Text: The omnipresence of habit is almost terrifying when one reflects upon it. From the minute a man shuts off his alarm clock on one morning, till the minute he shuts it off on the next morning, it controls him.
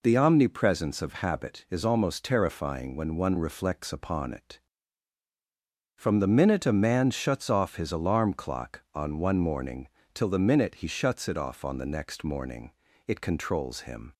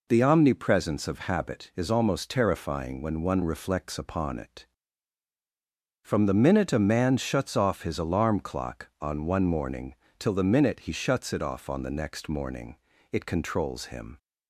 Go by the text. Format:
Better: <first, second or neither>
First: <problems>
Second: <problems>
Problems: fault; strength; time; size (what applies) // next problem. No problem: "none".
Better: neither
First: none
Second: none